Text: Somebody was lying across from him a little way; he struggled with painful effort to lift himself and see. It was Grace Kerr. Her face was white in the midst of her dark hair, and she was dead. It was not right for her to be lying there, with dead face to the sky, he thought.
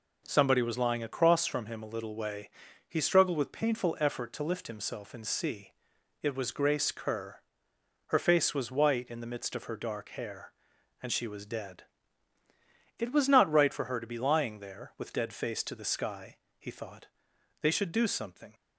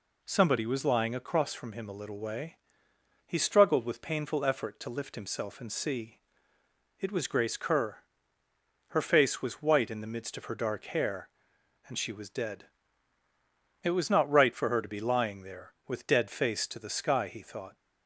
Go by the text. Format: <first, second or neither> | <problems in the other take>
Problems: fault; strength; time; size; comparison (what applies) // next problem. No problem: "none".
second | goes on to say "They should do something"; noticeable; from 17.6 s on; 0.94 s long